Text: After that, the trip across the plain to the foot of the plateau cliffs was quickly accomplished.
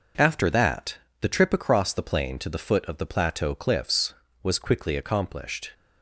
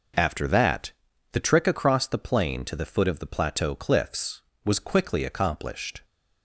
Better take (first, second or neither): first